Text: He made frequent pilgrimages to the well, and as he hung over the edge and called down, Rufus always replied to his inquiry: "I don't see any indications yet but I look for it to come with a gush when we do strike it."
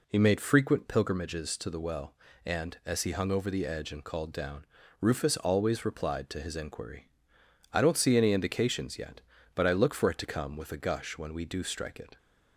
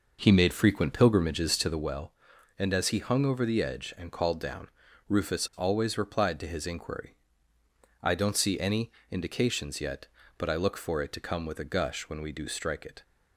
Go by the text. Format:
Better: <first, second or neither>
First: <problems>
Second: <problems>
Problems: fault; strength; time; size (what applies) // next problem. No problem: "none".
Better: first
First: none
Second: starts louder than the rest; noticeable; until 1.9 s; 5.5 dB // pauses between "any" and "indications"; slight; at 8.9 s; 0.20 s long